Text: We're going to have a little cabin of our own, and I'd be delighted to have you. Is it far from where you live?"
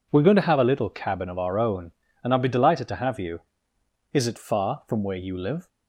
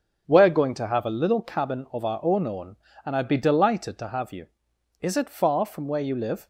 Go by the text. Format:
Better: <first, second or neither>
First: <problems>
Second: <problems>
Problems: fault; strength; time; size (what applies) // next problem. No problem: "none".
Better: first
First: none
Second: starts louder than the rest; strong; until 1.2 s; 7.5 dB // says "own" twice; at 2.4 s